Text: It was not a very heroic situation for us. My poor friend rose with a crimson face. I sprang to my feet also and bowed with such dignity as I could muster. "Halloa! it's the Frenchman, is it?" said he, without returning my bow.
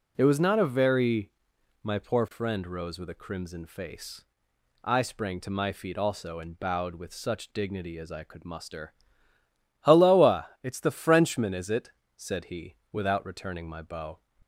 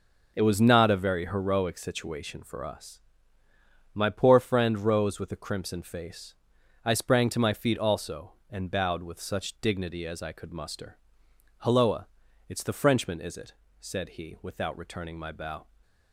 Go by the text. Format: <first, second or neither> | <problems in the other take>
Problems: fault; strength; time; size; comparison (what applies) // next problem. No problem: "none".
second | skips "heroic situation for us"; at 1.5 s